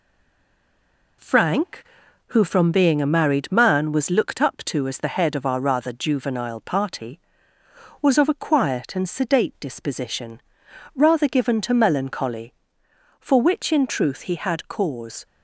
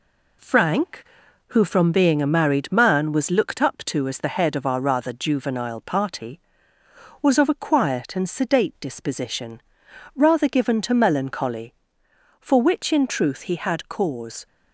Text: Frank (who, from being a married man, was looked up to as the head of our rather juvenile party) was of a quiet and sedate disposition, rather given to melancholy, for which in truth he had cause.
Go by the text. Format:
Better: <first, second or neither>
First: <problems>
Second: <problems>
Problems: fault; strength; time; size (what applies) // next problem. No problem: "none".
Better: second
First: stays silent before the first word; noticeable; until 1.1 s; 1.1 s long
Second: none